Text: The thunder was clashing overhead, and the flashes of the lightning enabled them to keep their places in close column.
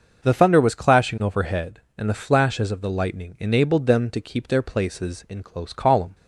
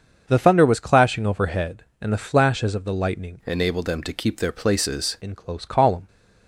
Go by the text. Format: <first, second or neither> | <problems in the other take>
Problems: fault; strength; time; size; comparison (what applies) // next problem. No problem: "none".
first | starts louder than the rest; until 1.2 s; 6.5 dB; noticeable in the first // changes voice from "enabled" to "places"; from 3.4 to 5.1 s; 1.7 s long